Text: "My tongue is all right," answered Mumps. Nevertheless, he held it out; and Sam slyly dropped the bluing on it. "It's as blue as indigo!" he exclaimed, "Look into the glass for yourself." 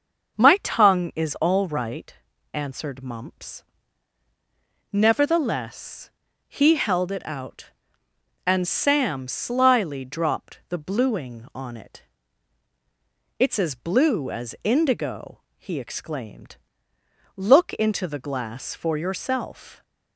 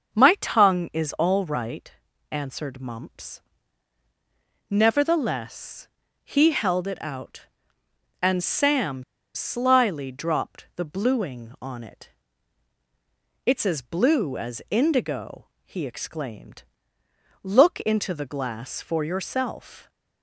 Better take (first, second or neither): first